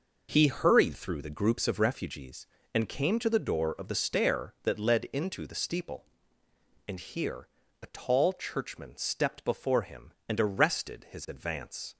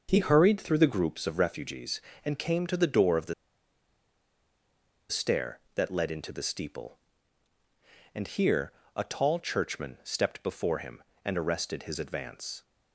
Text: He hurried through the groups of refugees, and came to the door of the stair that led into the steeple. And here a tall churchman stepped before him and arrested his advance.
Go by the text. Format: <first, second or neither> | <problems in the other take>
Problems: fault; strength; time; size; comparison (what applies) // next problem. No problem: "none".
first | pauses between "the" and "stair"; strong; at 3.3 s; 1.7 s long // pauses between "here" and "a"; slight; at 8.7 s; 0.24 s long; slight in the first